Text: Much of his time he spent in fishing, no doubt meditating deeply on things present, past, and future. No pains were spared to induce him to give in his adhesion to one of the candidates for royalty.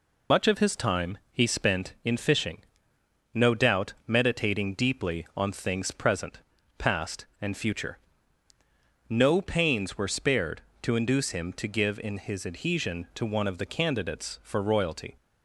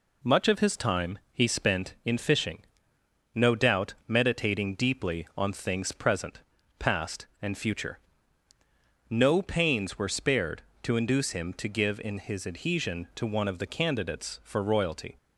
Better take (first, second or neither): second